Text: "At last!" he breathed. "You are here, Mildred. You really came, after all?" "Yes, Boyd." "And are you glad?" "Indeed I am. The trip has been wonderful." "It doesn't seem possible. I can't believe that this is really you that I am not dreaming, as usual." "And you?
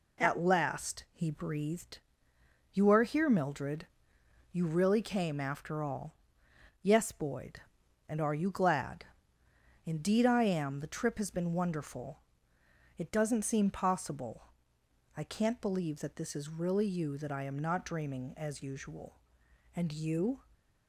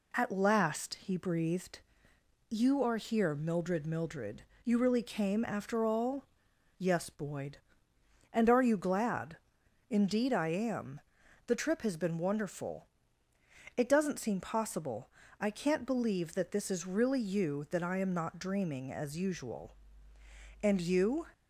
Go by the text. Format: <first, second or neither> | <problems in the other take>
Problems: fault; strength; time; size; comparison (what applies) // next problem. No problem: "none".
first | says "Mildred" twice; at 3.8 s